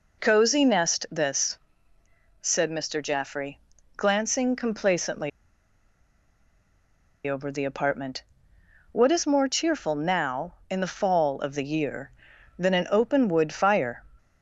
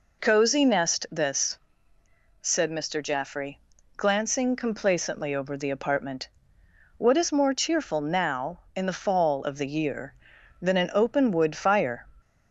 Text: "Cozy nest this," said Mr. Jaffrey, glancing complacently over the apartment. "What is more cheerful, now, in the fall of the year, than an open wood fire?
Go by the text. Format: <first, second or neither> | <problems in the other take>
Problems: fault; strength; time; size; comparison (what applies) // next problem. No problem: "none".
second | pauses between "complacently" and "over"; strong; at 5.2 s; 1.9 s long